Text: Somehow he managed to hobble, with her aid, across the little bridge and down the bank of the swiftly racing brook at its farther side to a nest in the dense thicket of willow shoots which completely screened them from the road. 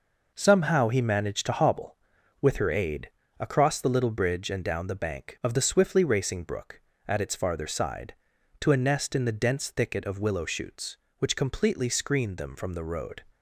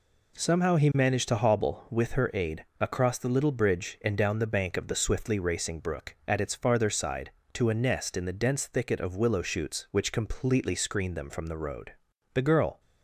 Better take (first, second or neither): first